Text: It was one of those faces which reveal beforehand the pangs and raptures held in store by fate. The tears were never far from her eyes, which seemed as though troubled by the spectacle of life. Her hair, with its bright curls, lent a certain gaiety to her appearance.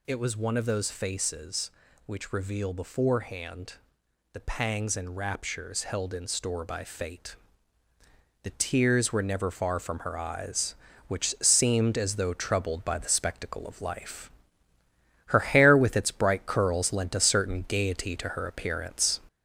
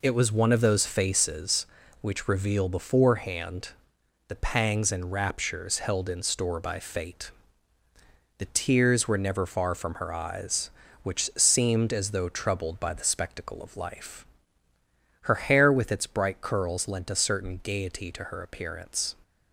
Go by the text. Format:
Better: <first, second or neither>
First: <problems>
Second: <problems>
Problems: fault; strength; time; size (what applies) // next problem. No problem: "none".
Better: second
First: gets louder; noticeable; throughout; 4.5 dB // pauses between "beforehand" and "the"; noticeable; at 3.7 s; 0.60 s long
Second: pauses between "beforehand" and "the"; noticeable; at 3.6 s; 0.60 s long